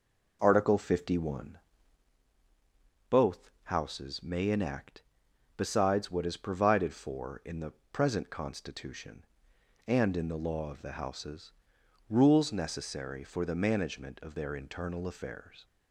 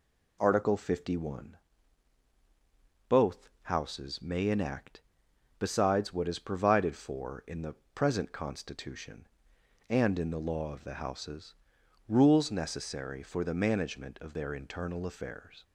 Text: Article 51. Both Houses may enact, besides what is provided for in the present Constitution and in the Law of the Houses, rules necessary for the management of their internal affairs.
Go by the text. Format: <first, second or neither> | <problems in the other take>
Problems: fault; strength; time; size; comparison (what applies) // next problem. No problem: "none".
second | starts louder than the rest; noticeable; until 2.2 s; 5 dB // pauses between "the" and "present"; slight; at 7.7 s; 0.18 s long; slight in the second